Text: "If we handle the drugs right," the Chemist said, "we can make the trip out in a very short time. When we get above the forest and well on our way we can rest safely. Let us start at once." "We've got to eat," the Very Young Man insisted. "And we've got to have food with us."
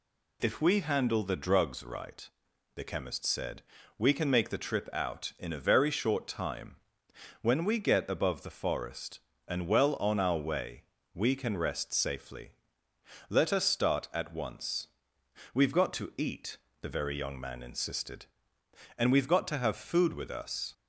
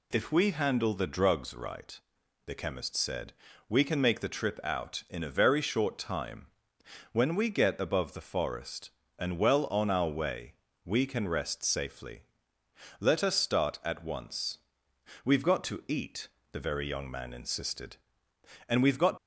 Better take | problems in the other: first | pauses between "way" and "we"; slight; at 10.5 s; 0.28 s long; slight in the first // stops before "to have food with us"; at 19.1 s

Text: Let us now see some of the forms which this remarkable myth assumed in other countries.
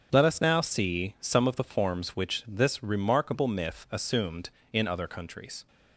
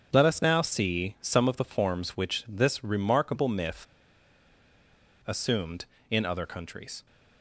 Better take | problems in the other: first | starts louder than the rest; strong; until 1.1 s; 7.5 dB; strong in the first // pauses between "myth" and "assumed"; strong; at 3.8 s; 1.4 s long

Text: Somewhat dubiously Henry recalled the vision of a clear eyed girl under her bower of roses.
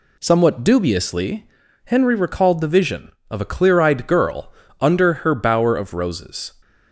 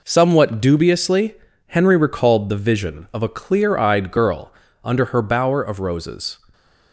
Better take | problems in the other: neither | pauses between "dubiously" and "Henry"; the same in both // pauses between "girl" and "under"; slight; the same in both

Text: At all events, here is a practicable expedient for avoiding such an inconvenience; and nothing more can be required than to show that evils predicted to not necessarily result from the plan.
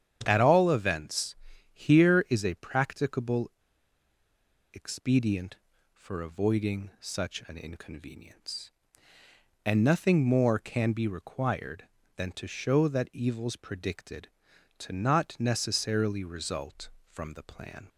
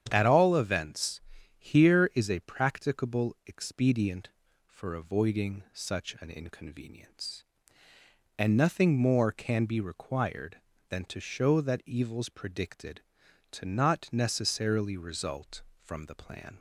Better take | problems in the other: second | starts louder than the rest; strong; until 1.2 s; 9 dB; strong in the second // pauses between "practicable" and "expedient"; at 3.4 s; 1.2 s long

